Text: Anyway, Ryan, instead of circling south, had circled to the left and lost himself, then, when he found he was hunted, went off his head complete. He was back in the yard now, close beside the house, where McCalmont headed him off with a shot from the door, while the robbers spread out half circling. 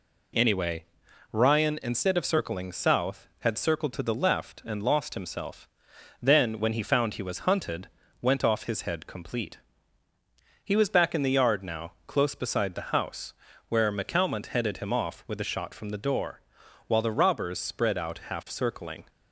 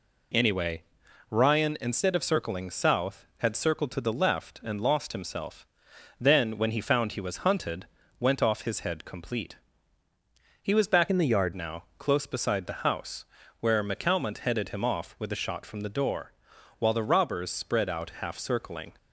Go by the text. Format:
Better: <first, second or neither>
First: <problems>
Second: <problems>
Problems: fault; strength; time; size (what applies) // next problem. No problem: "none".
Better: first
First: none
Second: changes voice from "in" to "yard"; from 11.0 to 11.5 s; 0.5 s long